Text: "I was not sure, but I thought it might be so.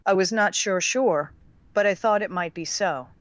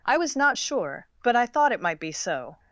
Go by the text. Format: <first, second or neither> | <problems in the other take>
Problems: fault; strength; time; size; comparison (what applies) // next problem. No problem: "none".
second | says "sure" twice; at 0.8 s